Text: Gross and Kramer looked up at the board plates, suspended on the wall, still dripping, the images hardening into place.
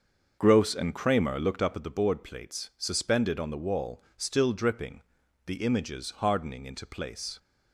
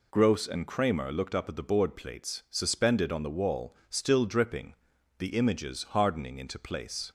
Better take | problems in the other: second | starts louder than the rest; until 1.9 s; 6.5 dB

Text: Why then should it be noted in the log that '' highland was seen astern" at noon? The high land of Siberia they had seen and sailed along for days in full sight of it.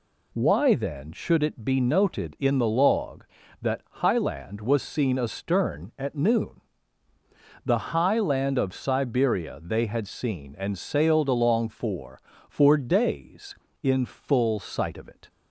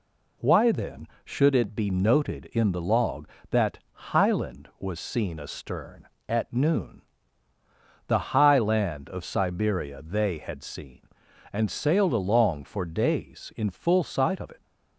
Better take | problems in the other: second | says "for" twice; at 12.4 s

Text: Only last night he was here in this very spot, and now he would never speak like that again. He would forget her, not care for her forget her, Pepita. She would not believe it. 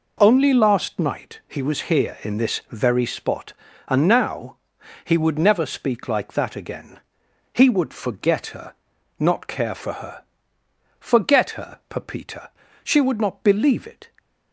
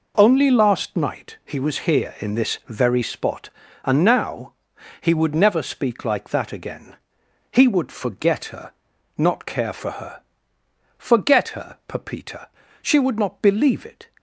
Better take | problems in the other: neither | pauses between "now" and "he"; noticeable; the same in both // pauses between "her" and "forget"; noticeable; the same in both

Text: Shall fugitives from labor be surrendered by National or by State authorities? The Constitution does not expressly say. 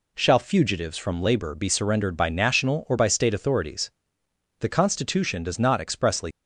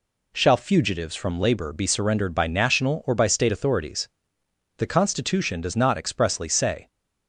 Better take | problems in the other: second | stops before "say"; at 6.3 s

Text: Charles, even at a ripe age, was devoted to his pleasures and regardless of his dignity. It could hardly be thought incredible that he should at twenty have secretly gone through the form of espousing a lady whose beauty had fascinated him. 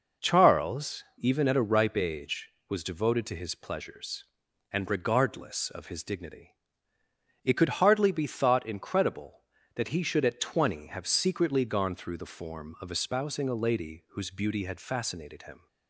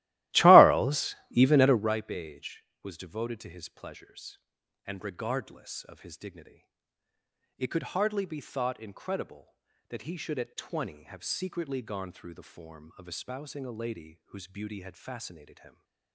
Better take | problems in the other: first | starts louder than the rest; strong; until 1.9 s; 17 dB

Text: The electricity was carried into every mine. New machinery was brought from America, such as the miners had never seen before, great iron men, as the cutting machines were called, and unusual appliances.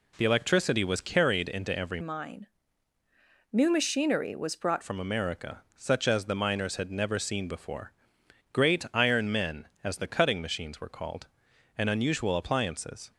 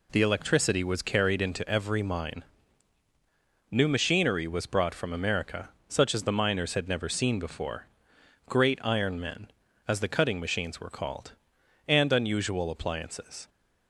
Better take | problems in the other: second | changes voice from "mine" to "brought"; from 2.0 to 4.8 s; 2.8 s long

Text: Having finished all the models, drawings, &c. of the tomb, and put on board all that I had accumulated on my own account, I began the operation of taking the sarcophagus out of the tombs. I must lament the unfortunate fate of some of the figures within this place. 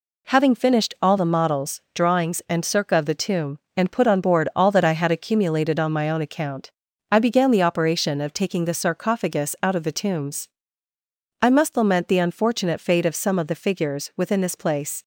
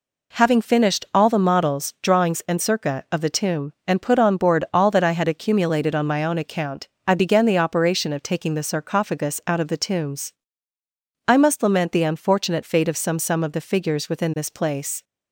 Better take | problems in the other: first | says "some" twice; at 13.1 s

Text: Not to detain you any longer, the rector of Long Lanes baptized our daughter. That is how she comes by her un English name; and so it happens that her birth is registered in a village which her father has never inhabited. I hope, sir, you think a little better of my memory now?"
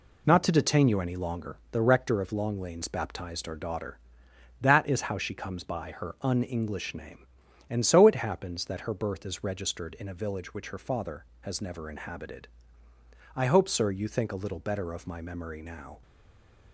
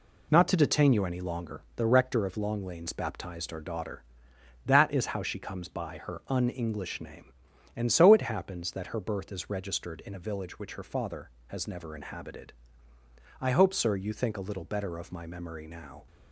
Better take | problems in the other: second | stays silent after the last word; slight; from 16.0 s on; 0.7 s long

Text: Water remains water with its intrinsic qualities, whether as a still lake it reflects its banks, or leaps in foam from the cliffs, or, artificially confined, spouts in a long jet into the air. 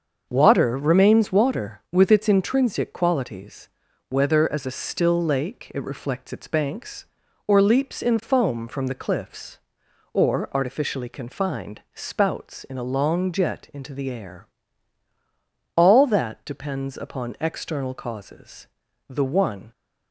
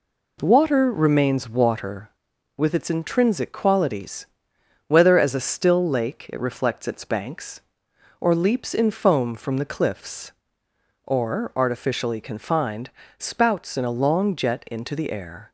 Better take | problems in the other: second | starts louder than the rest; until 1.3 s; 6.5 dB // goes on to say "All that depends upon external causes the one"; strong; from 15.7 s on; 3.9 s long

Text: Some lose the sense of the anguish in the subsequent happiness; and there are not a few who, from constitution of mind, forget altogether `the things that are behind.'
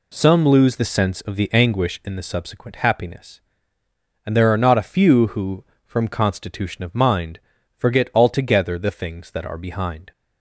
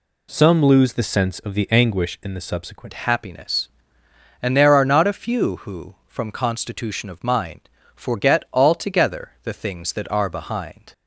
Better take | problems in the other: first | changes voice at "happiness"; from 2.9 s on; 8.0 s long

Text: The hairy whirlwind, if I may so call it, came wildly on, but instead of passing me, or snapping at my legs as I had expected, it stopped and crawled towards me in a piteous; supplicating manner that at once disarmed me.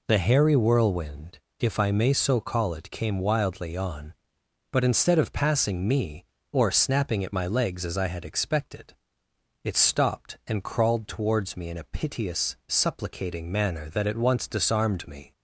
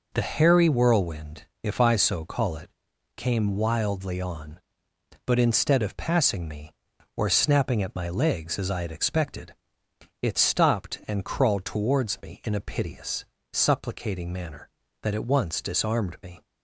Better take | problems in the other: first | skips "may"; at 1.9 s

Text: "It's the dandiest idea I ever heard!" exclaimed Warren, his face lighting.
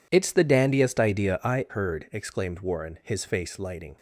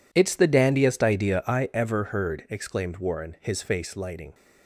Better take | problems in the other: second | skips "ever"; at 1.6 s

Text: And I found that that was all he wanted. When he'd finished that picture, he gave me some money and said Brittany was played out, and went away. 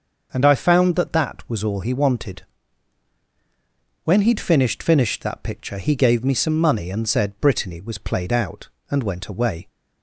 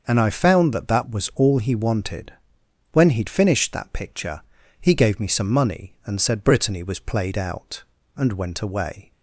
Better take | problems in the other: second | starts louder than the rest; until 1.3 s; 6 dB // says "finished" twice; at 4.8 s

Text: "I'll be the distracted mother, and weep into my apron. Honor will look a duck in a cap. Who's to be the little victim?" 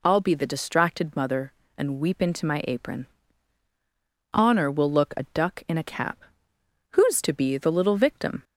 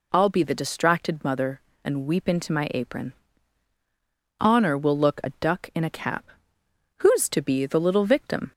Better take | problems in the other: neither | none

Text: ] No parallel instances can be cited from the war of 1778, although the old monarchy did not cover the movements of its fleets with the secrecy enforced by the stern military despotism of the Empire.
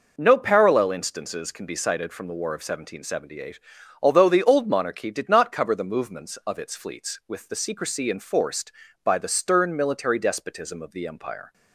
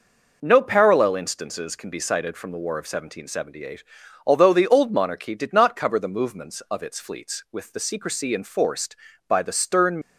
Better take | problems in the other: first | stops before "military despotism of the Empire"; at 10.0 s

